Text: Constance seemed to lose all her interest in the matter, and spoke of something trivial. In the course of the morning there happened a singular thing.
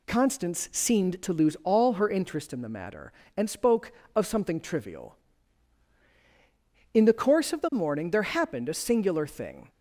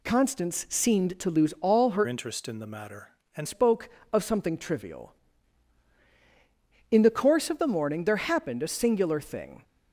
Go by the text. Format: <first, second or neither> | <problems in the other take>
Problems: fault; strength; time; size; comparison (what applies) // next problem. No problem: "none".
first | changes voice from "interest" to "and"; from 2.0 to 3.4 s; 1.4 s long